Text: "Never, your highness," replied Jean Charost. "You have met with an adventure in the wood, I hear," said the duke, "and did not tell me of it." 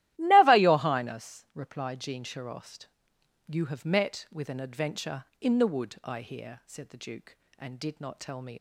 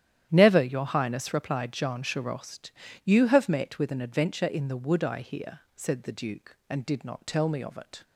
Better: second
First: starts louder than the rest; strong; until 1.2 s; 14.5 dB // stops before "of it"; at 8.5 s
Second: starts louder than the rest; strong; until 1.3 s; 11 dB

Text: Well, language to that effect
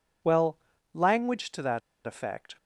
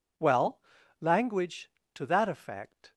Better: second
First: pauses between "that" and "effect"; slight; at 1.8 s; 0.24 s long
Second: none

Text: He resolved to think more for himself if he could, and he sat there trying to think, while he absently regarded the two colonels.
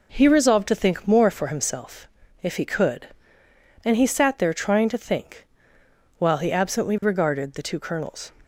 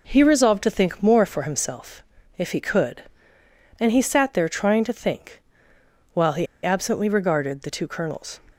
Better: first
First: pauses between "himself" and "if"; slight; at 2.0 s; 0.34 s long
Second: pauses between "himself" and "if"; slight; at 2.0 s; 0.34 s long // pauses between "he" and "absently"; slight; at 6.4 s; 0.17 s long

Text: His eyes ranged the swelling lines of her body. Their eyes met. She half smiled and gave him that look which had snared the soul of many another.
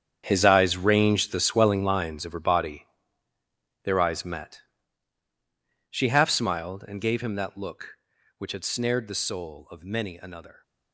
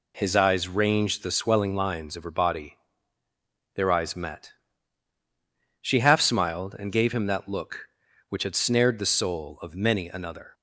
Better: second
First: gets quieter; strong; throughout; 14.5 dB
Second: none

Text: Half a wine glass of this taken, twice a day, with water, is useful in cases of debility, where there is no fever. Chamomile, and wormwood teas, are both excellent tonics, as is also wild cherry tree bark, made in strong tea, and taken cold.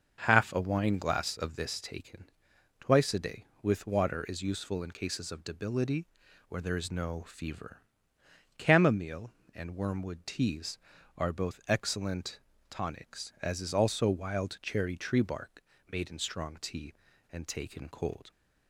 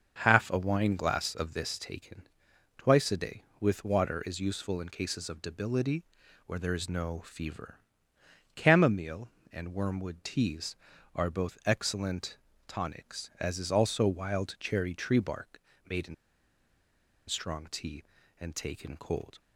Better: first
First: starts louder than the rest; until 1.2 s; 6.5 dB // pauses between "excellent" and "tonics"; slight; at 12.4 s; 0.28 s long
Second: starts louder than the rest; until 1.2 s; 6.5 dB // pauses between "excellent" and "tonics"; slight; at 12.3 s; 0.28 s long // pauses between "in" and "strong"; at 16.1 s; 1.1 s long

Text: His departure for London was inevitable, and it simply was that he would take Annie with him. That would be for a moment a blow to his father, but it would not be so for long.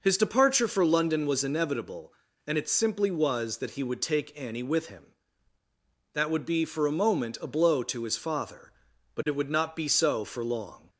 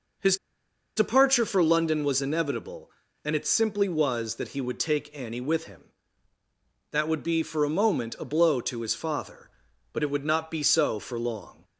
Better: first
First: none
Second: pauses between "His" and "departure"; noticeable; at 0.3 s; 0.61 s long

